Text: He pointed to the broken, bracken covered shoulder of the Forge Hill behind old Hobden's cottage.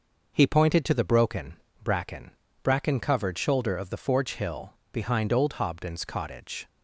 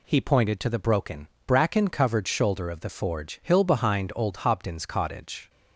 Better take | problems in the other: second | says "bracken" twice; at 2.6 s // pauses between "Hill" and "behind"; slight; at 4.7 s; 0.18 s long

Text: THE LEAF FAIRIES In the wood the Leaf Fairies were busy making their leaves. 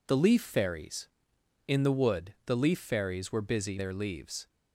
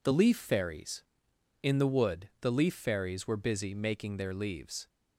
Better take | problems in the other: second | skips "making"; at 3.7 s

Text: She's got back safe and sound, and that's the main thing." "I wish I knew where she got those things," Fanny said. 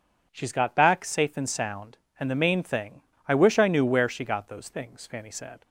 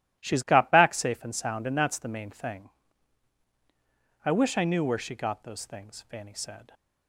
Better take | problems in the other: second | skips "that's"; at 2.3 s

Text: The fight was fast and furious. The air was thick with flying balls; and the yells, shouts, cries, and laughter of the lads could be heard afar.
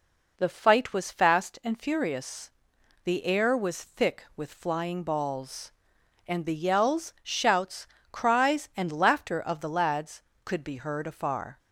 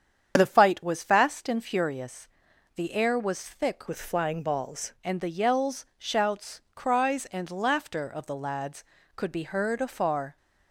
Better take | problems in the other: first | starts louder than the rest; strong; until 1.3 s; 8 dB // changes voice from "with" to "balls"; from 3.8 to 4.9 s; 1.1 s long

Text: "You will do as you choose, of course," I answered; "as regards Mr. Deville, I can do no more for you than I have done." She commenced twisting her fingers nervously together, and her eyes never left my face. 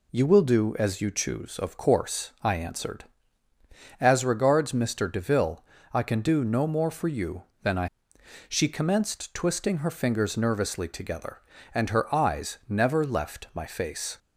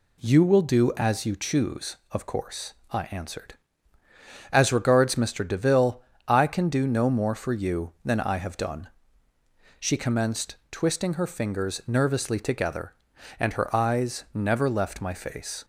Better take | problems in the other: second | skips "have done"; at 8.1 s

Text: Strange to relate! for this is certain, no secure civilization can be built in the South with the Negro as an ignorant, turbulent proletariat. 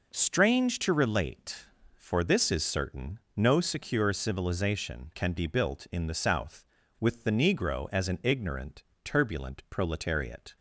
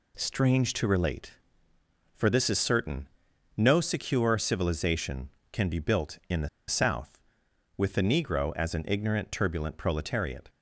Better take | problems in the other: first | pauses between "the" and "South"; slight; at 6.4 s; 0.20 s long

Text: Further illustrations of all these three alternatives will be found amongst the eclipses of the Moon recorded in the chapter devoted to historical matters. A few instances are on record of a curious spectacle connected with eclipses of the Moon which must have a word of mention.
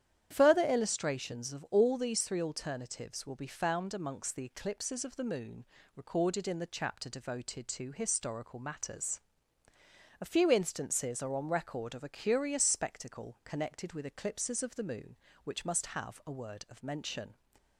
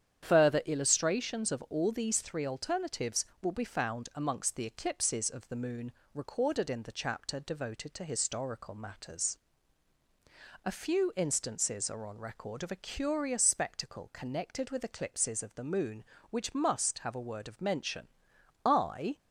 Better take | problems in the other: first | starts louder than the rest; strong; until 1.2 s; 9 dB; strong in the first // pauses between "Moon" and "recorded"; slight; at 5.9 s; 0.22 s long; slight in the first // goes on to say "I"; from 18.6 s on; 0.54 s long

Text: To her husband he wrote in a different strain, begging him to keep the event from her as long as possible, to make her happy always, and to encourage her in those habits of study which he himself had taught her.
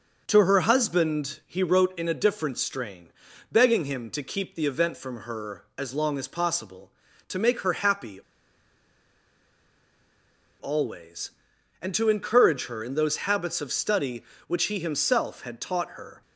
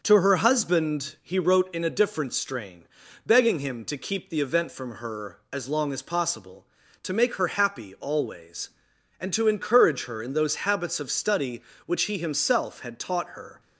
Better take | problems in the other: second | pauses between "happy" and "always"; strong; at 8.1 s; 2.4 s long

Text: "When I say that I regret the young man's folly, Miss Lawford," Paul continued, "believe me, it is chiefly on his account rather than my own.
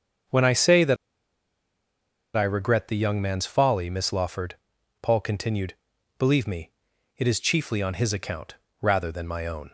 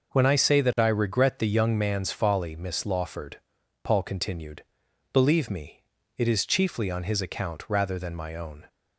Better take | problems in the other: second | starts louder than the rest; until 2.7 s; 7 dB // pauses between "that" and "I"; strong; at 0.9 s; 1.4 s long // pauses between "account" and "rather"; slight; at 8.5 s; 0.28 s long

